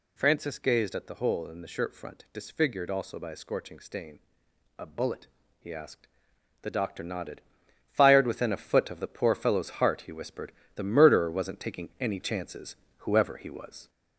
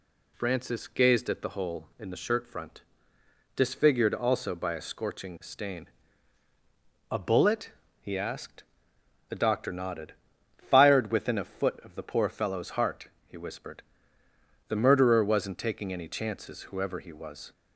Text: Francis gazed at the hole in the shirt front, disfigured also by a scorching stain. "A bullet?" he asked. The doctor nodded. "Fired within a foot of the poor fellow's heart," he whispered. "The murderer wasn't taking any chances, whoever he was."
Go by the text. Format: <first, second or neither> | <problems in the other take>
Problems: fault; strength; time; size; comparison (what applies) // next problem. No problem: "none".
second | gets louder; slight; throughout; 2.5 dB